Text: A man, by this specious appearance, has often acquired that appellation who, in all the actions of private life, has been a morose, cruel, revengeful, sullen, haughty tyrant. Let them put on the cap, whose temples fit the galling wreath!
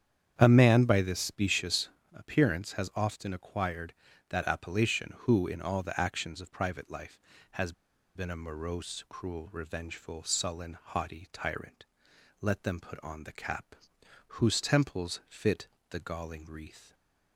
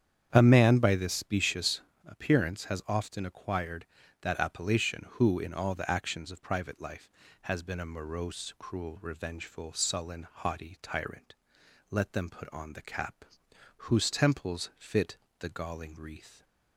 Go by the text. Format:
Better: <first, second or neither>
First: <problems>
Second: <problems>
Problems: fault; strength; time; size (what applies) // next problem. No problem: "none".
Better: second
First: starts louder than the rest; strong; until 1.4 s; 9 dB // pauses between "specious" and "appearance"; slight; at 1.8 s; 0.24 s long // pauses between "has" and "been"; at 7.7 s; 0.43 s long // pauses between "fit" and "the"; slight; at 15.6 s; 0.24 s long // stays silent after the last word; slight; from 16.8 s on; 0.5 s long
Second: starts louder than the rest; strong; until 1.3 s; 9 dB // pauses between "specious" and "appearance"; slight; at 1.8 s; 0.24 s long // pauses between "fit" and "the"; slight; at 15.1 s; 0.24 s long